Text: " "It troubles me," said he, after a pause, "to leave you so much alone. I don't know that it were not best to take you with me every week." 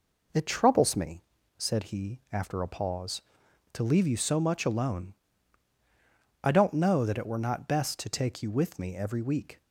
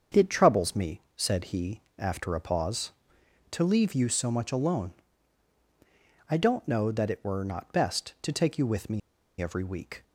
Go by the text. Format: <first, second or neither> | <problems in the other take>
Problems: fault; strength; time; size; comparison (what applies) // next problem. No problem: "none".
first | starts louder than the rest; until 1.2 s; 7 dB // pauses between "me" and "every"; at 9.0 s; 0.40 s long